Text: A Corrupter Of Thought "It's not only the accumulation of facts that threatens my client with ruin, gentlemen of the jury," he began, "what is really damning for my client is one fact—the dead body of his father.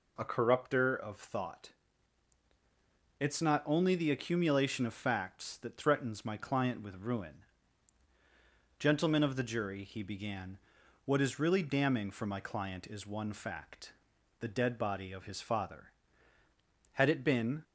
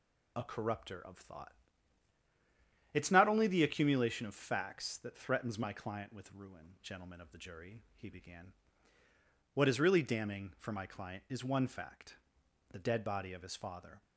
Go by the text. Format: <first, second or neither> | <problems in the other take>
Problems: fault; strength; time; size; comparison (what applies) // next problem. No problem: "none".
second | pauses between "Thought" and "It's"; strong; at 1.7 s; 1.4 s long; strong in the second // goes on to say "Had it been"; noticeable; from 16.9 s on; 0.70 s long